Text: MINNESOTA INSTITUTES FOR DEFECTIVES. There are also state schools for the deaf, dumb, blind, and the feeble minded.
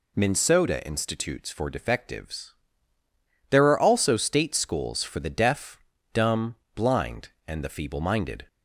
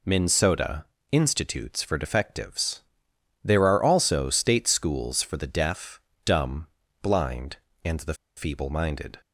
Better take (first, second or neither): first